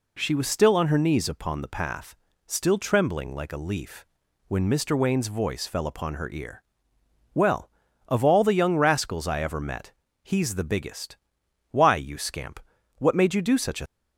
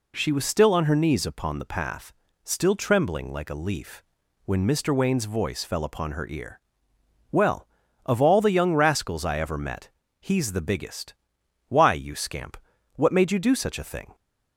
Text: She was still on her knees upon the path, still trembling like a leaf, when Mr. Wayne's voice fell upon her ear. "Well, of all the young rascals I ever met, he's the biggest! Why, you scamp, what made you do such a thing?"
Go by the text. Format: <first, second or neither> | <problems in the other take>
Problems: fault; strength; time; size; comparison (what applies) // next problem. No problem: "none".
second | stops before "thing"; at 13.8 s